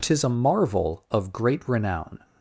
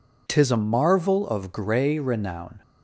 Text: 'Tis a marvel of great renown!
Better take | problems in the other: first | says "grey" for "great"; at 1.5 s

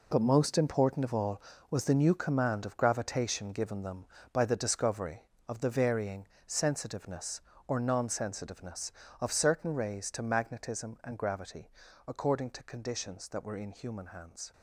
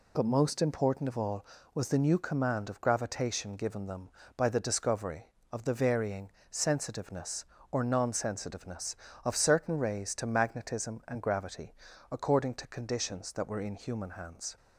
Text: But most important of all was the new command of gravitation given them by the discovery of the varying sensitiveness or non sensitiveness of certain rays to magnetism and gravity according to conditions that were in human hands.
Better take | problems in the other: second | gets quieter; strong; throughout; 12 dB // pauses between "varying" and "sensitiveness"; slight; at 6.2 s; 0.18 s long; slight in the second // pauses between "gravity" and "according"; slight; at 11.7 s; 0.36 s long; slight in the second

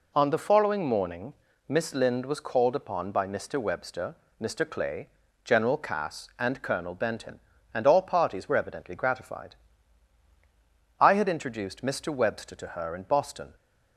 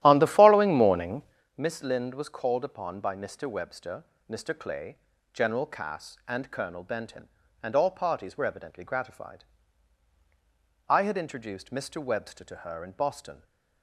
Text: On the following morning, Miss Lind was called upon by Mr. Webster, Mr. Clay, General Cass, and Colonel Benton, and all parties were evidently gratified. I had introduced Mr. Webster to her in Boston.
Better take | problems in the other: first | starts louder than the rest; strong; until 1.5 s; 13.5 dB

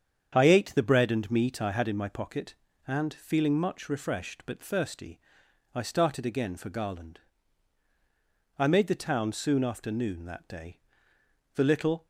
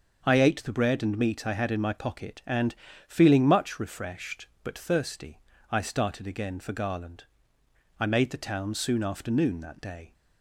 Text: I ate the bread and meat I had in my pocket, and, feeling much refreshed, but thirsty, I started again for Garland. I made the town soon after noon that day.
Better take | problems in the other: second | starts louder than the rest; strong; until 1.3 s; 8 dB; also in the second // goes on to say "The little"; from 11.5 s on; 0.52 s long

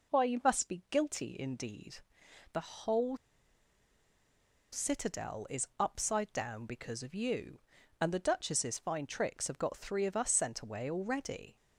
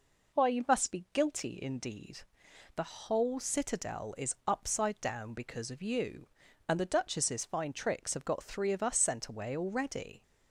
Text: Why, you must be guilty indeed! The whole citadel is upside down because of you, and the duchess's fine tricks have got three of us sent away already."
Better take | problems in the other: second | pauses between "whole" and "citadel"; strong; at 3.1 s; 1.5 s long

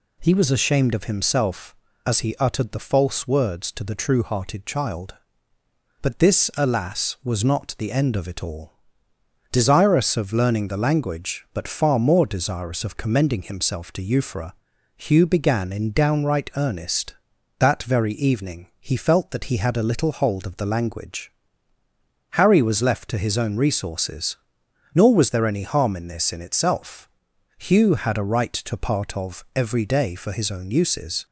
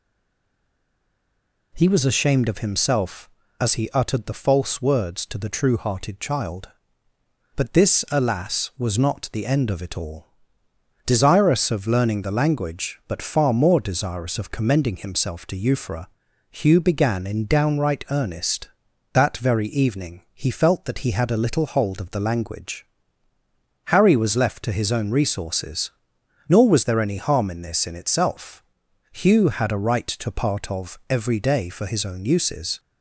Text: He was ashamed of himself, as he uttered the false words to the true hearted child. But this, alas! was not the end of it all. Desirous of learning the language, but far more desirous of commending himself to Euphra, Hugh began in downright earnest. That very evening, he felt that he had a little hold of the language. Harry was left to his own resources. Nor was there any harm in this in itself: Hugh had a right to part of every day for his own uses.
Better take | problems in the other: first | stays silent before the first word; noticeable; until 1.7 s; 1.7 s long

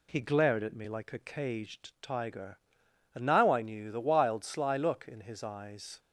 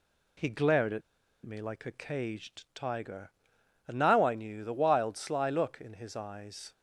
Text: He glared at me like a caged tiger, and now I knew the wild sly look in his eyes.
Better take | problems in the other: first | pauses between "at" and "me"; at 1.0 s; 0.44 s long

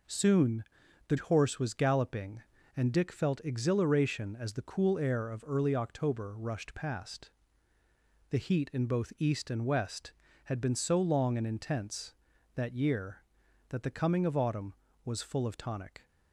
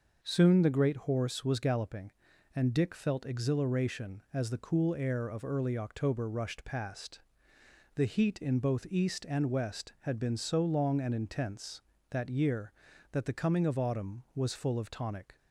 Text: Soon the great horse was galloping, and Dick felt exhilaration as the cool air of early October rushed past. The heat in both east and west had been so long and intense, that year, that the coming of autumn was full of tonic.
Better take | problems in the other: second | pauses between "Soon" and "the"; at 0.6 s; 0.44 s long // skips "great"; at 1.1 s

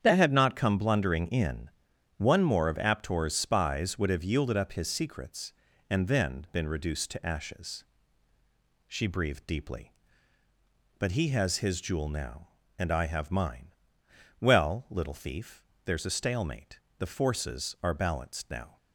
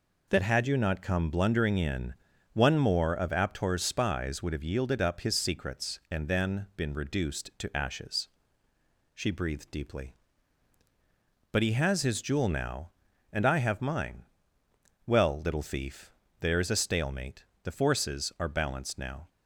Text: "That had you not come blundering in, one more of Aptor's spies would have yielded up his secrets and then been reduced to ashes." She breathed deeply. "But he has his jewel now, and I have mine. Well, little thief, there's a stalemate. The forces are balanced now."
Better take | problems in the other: second | starts louder than the rest; strong; until 1.0 s; 8.5 dB // skips "you"; at 0.3 s

